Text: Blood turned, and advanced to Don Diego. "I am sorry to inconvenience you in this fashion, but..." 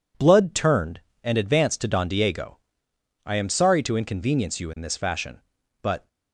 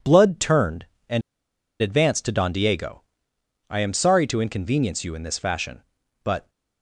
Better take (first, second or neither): first